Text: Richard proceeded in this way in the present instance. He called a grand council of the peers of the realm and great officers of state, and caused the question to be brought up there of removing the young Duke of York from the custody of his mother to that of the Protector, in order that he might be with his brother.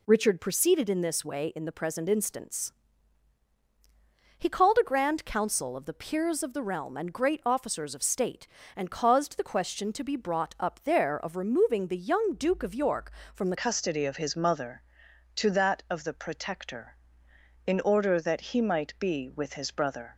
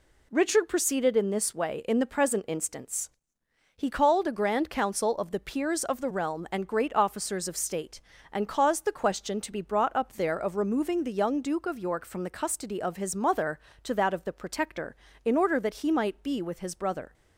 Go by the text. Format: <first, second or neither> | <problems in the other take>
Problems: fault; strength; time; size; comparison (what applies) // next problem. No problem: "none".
second | changes voice at "custody"; from 13.5 s on; 6.6 s long